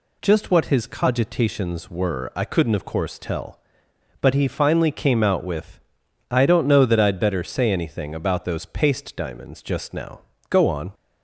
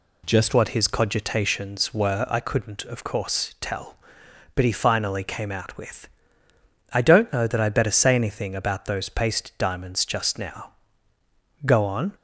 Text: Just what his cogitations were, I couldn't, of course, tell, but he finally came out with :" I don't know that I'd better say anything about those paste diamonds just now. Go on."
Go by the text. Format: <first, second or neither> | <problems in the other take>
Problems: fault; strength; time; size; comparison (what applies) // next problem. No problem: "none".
first | changes voice at "what"; from 0.5 s on; 11.6 s long